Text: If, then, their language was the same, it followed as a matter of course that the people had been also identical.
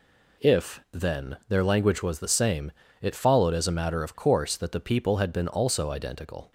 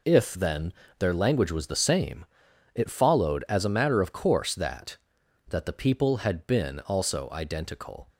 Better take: first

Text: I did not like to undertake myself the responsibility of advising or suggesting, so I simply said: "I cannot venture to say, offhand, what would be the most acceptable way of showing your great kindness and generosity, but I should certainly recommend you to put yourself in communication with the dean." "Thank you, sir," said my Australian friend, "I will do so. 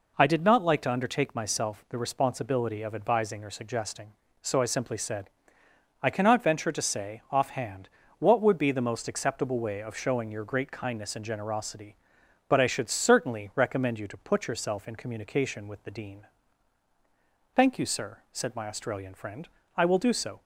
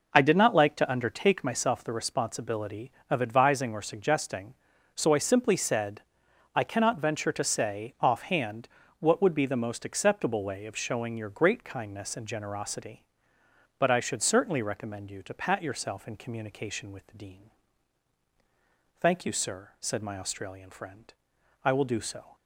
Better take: first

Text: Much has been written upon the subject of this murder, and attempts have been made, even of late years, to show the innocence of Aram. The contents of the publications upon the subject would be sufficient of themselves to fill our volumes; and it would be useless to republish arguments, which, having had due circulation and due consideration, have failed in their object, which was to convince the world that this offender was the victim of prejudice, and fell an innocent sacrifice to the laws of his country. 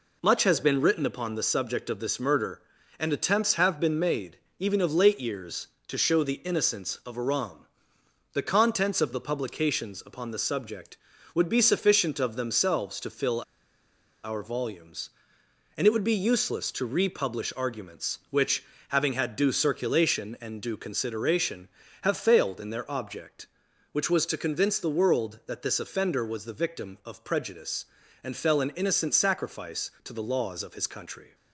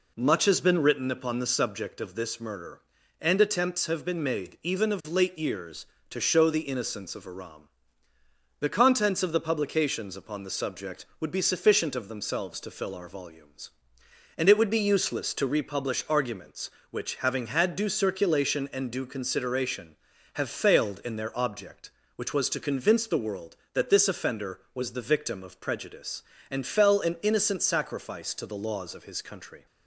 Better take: second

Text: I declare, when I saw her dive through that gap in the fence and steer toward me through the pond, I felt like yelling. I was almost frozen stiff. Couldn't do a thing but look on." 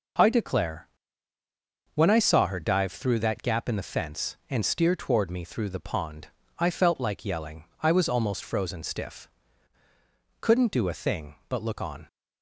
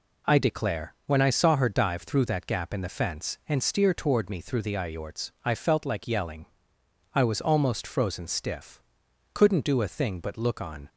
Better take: first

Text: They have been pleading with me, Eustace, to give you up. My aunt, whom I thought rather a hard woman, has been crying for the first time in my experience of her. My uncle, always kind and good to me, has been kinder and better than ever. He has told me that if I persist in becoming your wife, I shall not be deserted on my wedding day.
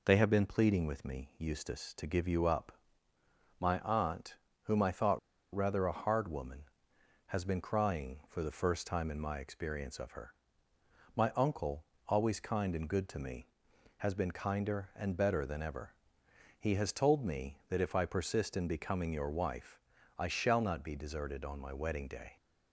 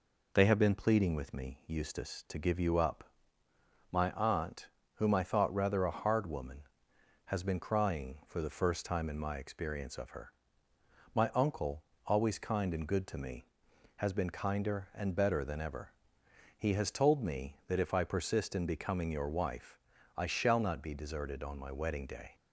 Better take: second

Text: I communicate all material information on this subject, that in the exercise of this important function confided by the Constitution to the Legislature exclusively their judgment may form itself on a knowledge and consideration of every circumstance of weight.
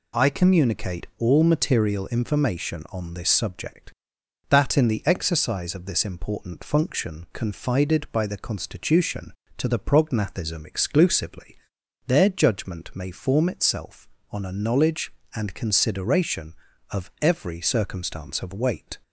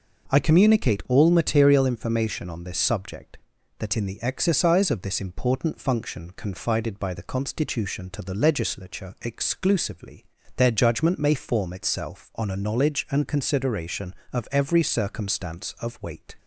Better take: second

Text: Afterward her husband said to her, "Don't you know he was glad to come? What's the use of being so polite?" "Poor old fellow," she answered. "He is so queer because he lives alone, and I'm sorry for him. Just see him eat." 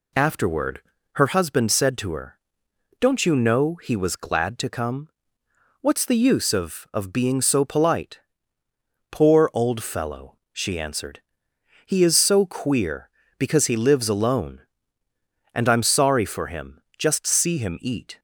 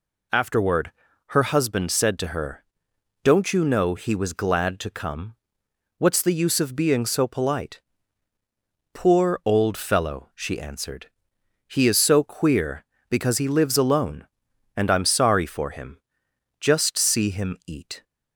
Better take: second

